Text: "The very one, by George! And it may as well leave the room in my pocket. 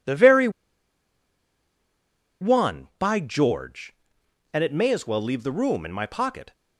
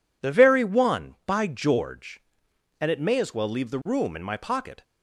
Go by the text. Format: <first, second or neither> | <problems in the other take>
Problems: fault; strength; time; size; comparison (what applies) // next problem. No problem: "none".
second | pauses between "very" and "one"; strong; at 0.4 s; 1.9 s long